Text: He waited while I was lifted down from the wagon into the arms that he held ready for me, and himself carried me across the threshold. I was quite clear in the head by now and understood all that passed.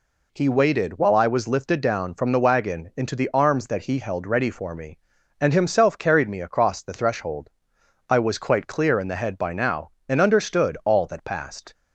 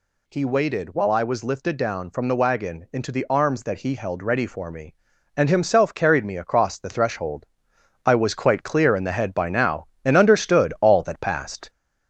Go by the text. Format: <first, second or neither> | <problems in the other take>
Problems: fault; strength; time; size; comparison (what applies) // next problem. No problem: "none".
first | gets louder; throughout; 4 dB